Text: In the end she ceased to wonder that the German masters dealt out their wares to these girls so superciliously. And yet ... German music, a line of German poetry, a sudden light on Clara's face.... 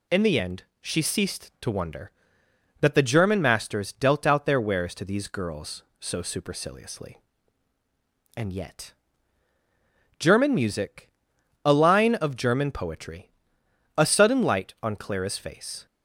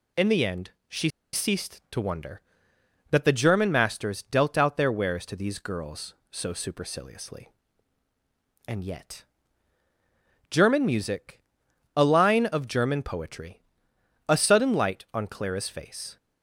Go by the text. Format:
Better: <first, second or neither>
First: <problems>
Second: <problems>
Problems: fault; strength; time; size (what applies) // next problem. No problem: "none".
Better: first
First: pauses between "end" and "she"; slight; at 0.6 s; 0.18 s long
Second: pauses between "end" and "she"; slight; at 0.6 s; 0.18 s long // pauses between "she" and "ceased"; slight; at 1.0 s; 0.23 s long